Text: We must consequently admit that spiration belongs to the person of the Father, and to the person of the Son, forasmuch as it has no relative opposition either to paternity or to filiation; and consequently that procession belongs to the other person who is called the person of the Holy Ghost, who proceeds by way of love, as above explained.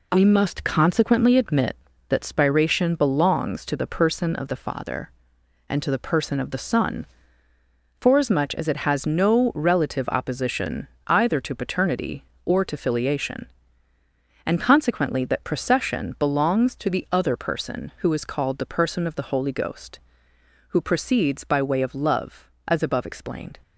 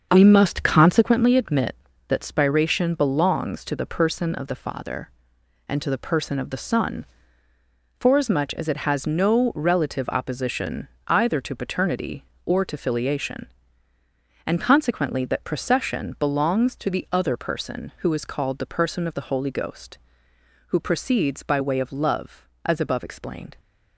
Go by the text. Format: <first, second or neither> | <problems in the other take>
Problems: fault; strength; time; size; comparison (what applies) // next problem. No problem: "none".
first | starts louder than the rest; until 1.1 s; 7 dB // pauses between "opposition" and "either"; slight; at 10.8 s; 0.22 s long; slight in the first